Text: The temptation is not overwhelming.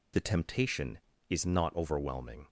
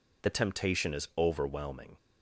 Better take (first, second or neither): first